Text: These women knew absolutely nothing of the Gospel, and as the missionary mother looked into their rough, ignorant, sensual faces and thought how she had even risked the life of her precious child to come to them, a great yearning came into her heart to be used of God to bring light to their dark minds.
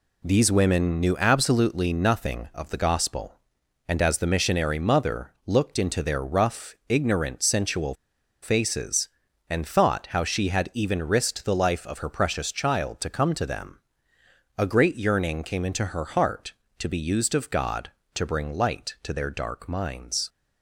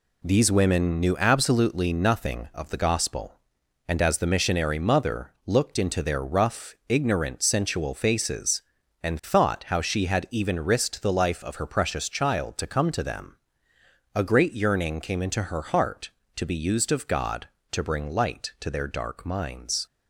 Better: second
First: pauses between "mother" and "looked"; slight; at 5.3 s; 0.16 s long // pauses between "sensual" and "faces"; noticeable; at 7.9 s; 0.50 s long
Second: pauses between "mother" and "looked"; slight; at 5.3 s; 0.16 s long

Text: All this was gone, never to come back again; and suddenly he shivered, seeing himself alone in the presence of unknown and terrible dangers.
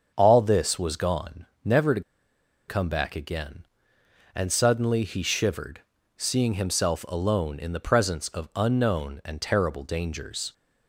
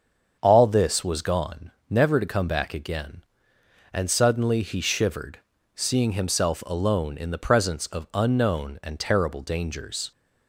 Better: second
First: starts louder than the rest; until 1.1 s; 7 dB // pauses between "to" and "come"; noticeable; at 2.0 s; 0.67 s long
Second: starts louder than the rest; strong; until 1.4 s; 7 dB

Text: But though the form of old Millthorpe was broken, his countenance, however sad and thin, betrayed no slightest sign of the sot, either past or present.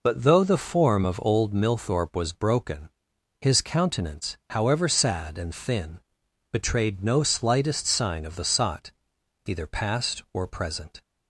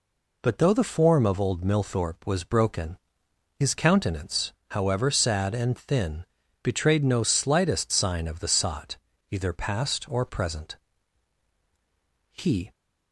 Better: first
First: none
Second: goes on to say "He"; slight; from 12.3 s on; 0.40 s long

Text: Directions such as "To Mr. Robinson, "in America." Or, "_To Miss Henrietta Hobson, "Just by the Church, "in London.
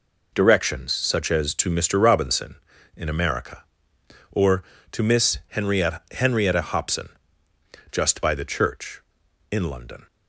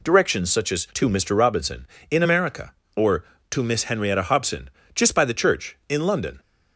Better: second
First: says "Henrietta" twice; at 6.1 s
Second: none

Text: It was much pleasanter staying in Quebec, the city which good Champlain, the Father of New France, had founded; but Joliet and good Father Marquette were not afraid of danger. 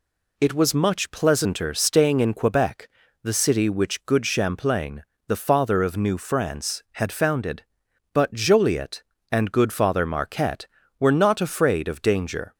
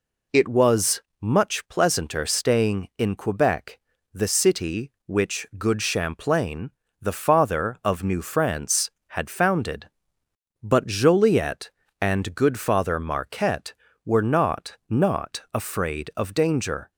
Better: first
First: none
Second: pauses between "was" and "much"; slight; at 1.0 s; 0.18 s long // says "not" twice; at 14.8 s

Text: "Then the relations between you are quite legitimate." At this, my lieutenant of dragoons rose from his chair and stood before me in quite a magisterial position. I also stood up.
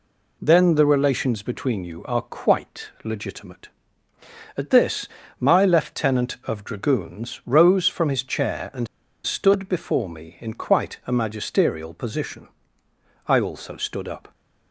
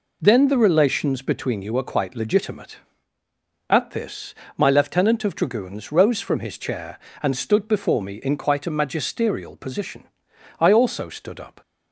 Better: second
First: pauses between "and" and "stood"; at 8.8 s; 0.37 s long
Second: none

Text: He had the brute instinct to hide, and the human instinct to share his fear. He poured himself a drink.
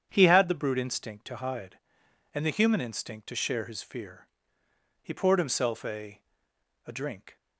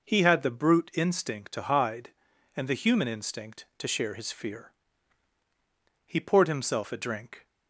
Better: second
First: starts louder than the rest; strong; until 1.1 s; 8.5 dB // says "a" twice; at 6.8 s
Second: none

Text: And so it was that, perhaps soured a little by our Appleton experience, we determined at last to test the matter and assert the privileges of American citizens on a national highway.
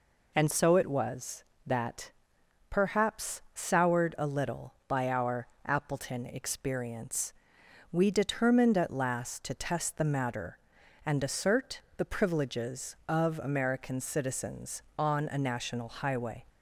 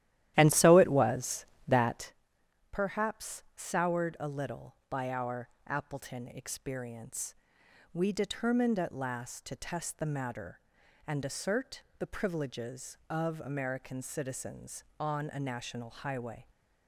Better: first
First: pauses between "our" and "Appleton"; slight; at 5.4 s; 0.18 s long // pauses between "assert" and "the"; slight; at 11.8 s; 0.16 s long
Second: starts louder than the rest; strong; until 2.2 s; 13 dB // pauses between "our" and "Appleton"; slight; at 5.4 s; 0.18 s long // pauses between "assert" and "the"; slight; at 11.8 s; 0.16 s long

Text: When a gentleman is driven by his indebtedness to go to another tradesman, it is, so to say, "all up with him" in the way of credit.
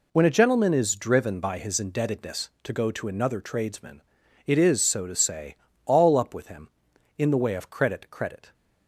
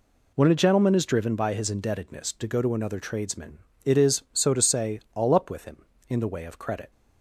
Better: second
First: says "credit" twice; at 8.0 s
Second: none

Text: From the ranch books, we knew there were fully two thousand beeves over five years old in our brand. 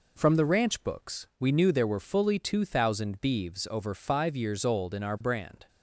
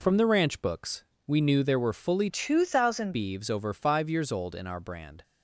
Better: first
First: none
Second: changes voice from "two" to "thousand"; from 2.2 to 3.1 s; 0.9 s long

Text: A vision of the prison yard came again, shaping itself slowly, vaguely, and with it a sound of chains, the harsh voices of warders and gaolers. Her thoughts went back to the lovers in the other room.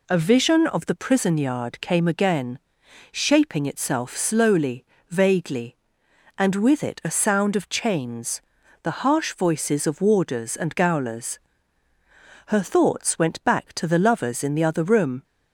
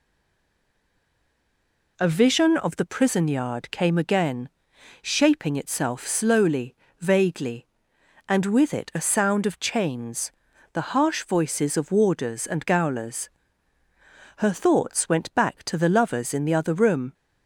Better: first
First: none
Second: stays silent before the first word; noticeable; until 1.9 s; 1.9 s long

